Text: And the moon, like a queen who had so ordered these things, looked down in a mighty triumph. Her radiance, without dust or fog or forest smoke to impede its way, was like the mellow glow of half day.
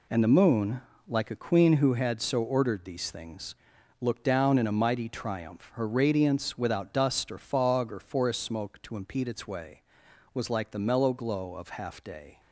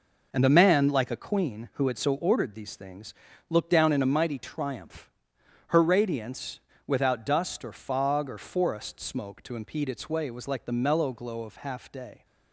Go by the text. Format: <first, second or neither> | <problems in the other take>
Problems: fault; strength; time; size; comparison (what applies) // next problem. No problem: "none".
first | says "man" for "moon"; at 0.5 s